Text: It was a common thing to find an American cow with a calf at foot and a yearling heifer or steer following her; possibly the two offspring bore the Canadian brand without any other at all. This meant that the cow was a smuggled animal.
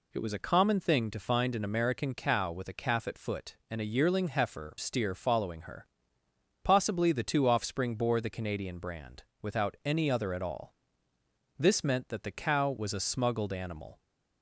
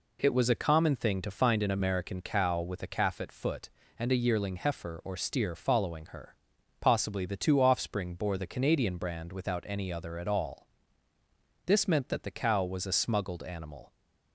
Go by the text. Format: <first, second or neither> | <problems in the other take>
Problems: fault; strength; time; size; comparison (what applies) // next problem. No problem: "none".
second | skips "or"; at 4.7 s // pauses between "brand" and "without"; slight; at 9.2 s; 0.18 s long